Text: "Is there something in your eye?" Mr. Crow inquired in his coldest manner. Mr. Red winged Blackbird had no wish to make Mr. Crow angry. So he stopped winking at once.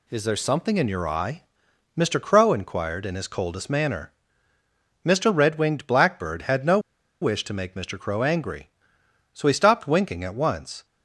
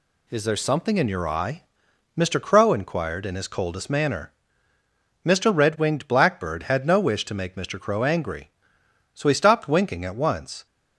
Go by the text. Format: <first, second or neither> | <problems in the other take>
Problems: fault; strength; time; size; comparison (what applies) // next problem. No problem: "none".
second | pauses between "no" and "wish"; at 6.7 s; 0.42 s long